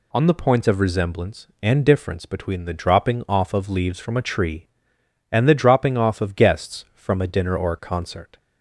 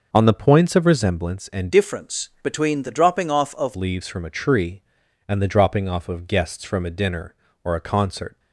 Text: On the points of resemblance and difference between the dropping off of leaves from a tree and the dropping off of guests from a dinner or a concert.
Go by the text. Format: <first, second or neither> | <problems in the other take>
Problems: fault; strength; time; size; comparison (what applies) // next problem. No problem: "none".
first | changes voice from "difference" to "of"; from 1.7 to 3.7 s; 2.0 s long